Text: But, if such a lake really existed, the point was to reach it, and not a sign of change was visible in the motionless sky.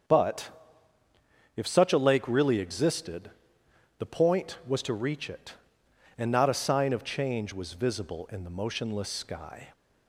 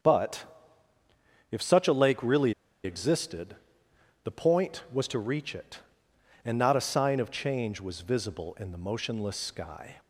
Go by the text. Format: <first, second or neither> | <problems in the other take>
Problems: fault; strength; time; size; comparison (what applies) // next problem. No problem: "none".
first | starts louder than the rest; strong; until 2.0 s; 7.5 dB; strong in the first // pauses between "really" and "existed"; slight; at 2.5 s; 0.30 s long